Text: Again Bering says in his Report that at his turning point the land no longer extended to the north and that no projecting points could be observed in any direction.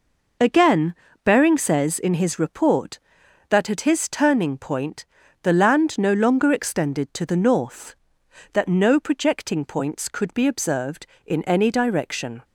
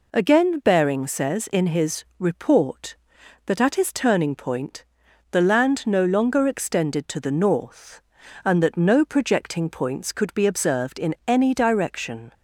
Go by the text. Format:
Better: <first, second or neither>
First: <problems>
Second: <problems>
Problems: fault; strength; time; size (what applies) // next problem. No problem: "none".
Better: second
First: pauses between "Again" and "Bering"; slight; at 0.9 s; 0.28 s long // pauses between "point" and "the"; at 5.0 s; 0.38 s long // skips "and"; at 8.2 s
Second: pauses between "point" and "the"; noticeable; at 4.8 s; 0.48 s long